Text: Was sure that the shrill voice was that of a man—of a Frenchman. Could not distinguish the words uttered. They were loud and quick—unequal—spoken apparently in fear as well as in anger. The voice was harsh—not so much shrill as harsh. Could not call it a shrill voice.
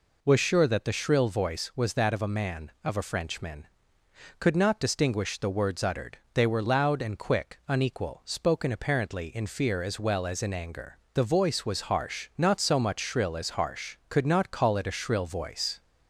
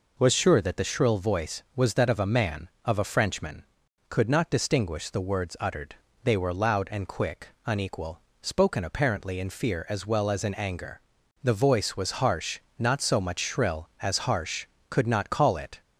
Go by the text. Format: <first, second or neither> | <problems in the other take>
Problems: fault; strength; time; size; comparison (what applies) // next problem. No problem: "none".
first | stops before "a shrill voice"; at 15.8 s